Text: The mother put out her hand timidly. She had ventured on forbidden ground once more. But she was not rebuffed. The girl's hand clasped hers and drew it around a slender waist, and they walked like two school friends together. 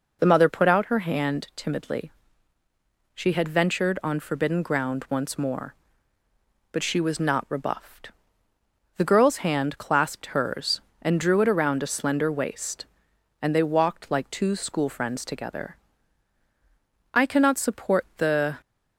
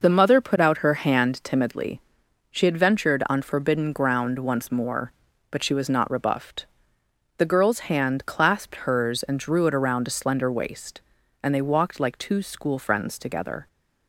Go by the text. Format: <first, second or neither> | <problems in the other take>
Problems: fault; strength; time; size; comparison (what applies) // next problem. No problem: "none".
second | goes on to say "I cannot support the"; from 17.1 s on; 1.4 s long